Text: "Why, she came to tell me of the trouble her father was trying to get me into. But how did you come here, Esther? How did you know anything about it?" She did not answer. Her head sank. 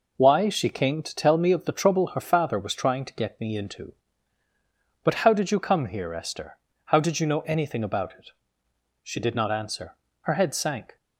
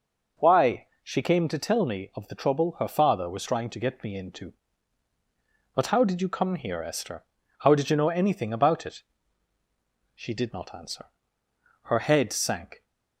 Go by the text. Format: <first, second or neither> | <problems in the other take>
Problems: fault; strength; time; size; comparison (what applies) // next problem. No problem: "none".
neither | none